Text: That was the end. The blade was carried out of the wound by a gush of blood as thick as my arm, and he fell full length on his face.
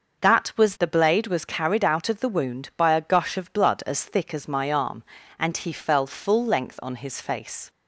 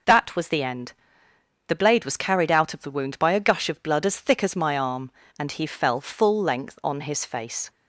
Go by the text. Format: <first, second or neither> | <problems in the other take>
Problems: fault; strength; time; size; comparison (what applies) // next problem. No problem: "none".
second | starts louder than the rest; until 1.2 s; 6 dB // skips "the end"; at 0.7 s